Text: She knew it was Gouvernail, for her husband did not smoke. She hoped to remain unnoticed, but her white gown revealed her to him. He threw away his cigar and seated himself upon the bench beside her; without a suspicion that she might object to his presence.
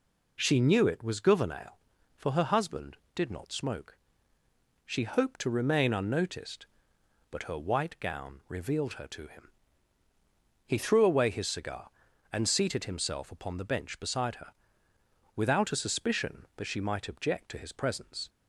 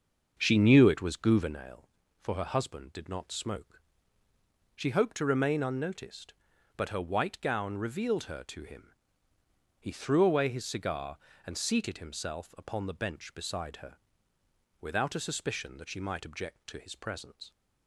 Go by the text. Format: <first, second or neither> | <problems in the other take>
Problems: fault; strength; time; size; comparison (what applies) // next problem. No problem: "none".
first | starts louder than the rest; until 1.6 s; 6.5 dB